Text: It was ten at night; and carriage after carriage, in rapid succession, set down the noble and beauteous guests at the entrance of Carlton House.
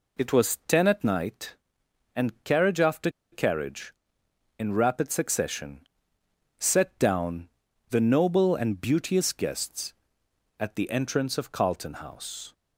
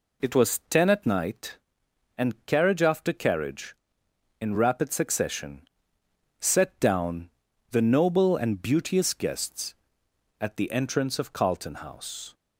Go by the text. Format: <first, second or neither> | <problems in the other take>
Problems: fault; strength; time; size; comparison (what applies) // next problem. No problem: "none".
second | pauses between "after" and "carriage"; slight; at 3.1 s; 0.21 s long // pauses between "down" and "the"; at 7.4 s; 0.40 s long; also in the second